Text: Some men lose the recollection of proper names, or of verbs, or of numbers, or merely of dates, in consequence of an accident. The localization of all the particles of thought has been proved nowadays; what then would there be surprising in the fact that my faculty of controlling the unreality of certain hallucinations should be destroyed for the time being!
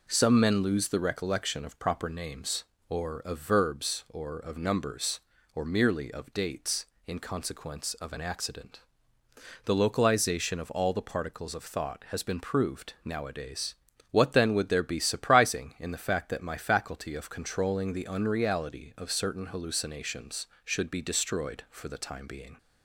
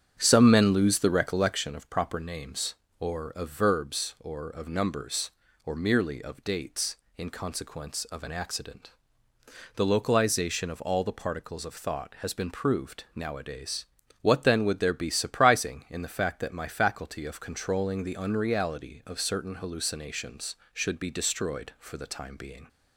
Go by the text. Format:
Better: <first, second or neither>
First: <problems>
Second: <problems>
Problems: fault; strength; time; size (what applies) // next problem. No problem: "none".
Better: first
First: none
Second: starts louder than the rest; strong; until 1.6 s; 9 dB